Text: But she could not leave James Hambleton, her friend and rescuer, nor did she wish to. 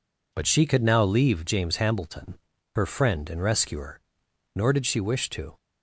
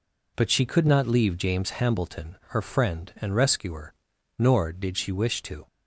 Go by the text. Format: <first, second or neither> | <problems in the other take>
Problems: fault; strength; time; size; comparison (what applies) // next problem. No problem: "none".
second | says "now" for "not"; at 0.8 s